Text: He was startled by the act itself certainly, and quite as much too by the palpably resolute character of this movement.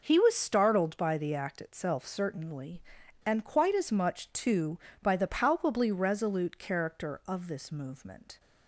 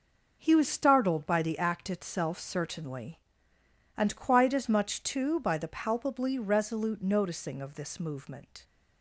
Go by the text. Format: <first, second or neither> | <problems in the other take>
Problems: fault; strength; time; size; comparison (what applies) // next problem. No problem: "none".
first | says "noticing" for "character"; at 7.0 s